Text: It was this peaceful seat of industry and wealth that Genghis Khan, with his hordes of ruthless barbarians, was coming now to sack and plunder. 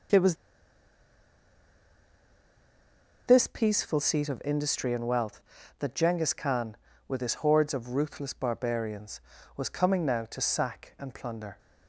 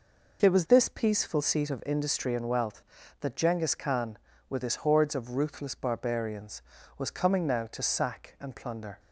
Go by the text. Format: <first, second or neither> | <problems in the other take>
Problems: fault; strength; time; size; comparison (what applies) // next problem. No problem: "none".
second | pauses between "was" and "this"; strong; at 0.3 s; 2.9 s long